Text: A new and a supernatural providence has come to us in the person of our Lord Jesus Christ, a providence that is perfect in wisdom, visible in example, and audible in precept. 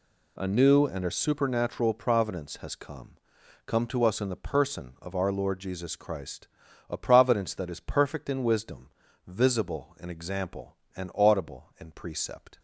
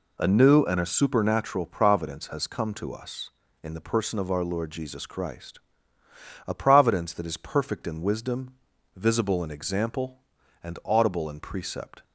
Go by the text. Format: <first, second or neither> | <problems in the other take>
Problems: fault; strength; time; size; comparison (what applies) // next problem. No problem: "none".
second | says "come" twice; at 3.6 s